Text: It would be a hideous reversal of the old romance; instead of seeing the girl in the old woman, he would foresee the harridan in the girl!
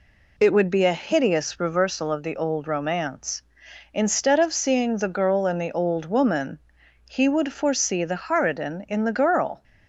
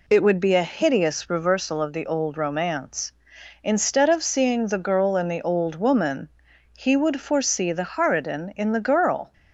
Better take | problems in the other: neither | none

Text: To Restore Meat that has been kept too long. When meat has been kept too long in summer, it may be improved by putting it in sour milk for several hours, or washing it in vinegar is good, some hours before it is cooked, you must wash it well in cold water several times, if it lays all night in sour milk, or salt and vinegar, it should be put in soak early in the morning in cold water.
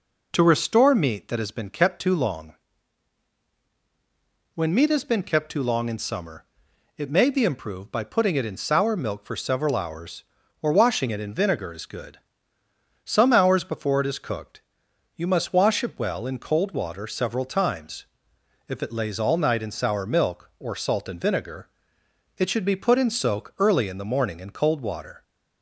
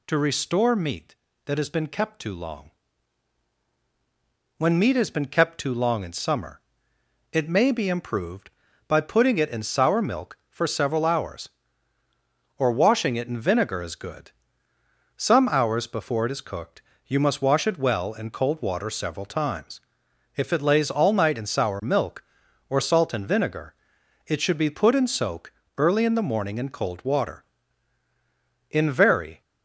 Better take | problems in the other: first | pauses between "soak" and "early"; slight; at 25.5 s; 0.28 s long // goes on to say "In very"; noticeable; from 28.6 s on; 0.72 s long

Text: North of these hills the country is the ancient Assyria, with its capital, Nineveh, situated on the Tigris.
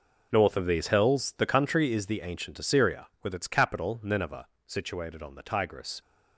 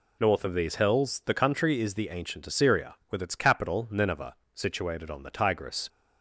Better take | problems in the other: second | gets quieter; strong; throughout; 13.5 dB

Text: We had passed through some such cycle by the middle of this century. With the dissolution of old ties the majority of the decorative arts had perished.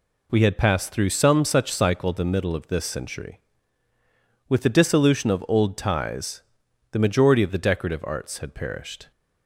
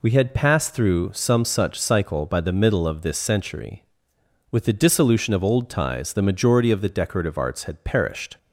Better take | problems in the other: second | skips "by"; at 2.1 s // pauses between "ties" and "the"; noticeable; at 6.4 s; 0.52 s long

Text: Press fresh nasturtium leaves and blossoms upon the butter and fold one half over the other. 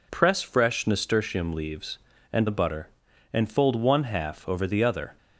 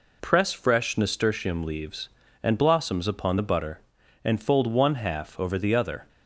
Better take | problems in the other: second | skips "blossoms upon"; at 2.4 s

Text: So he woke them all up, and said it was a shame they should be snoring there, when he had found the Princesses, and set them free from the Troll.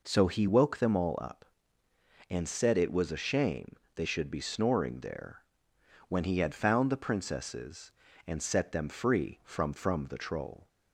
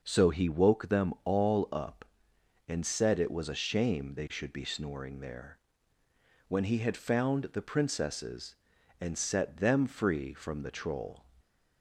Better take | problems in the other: second | pauses between "shame" and "they"; slight; at 3.7 s; 0.22 s long // says "from" twice; at 9.7 s

